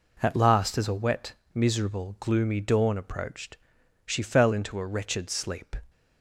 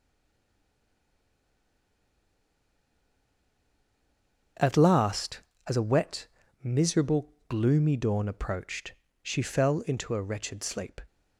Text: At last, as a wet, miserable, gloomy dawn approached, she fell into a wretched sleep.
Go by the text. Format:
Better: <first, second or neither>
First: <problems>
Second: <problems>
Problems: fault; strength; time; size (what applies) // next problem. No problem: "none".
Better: first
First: none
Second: stays silent before the first word; strong; until 4.5 s; 4.5 s long // starts louder than the rest; until 5.8 s; 6.5 dB